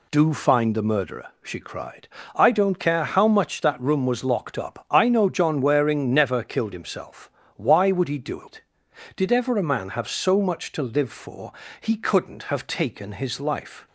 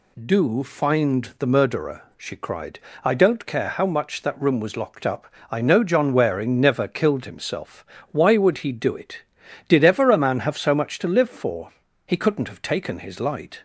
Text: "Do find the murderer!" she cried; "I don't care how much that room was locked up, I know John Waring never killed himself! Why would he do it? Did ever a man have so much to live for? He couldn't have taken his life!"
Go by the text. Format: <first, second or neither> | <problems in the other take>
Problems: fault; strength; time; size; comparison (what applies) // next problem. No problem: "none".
first | says "light" for "life"; at 13.2 s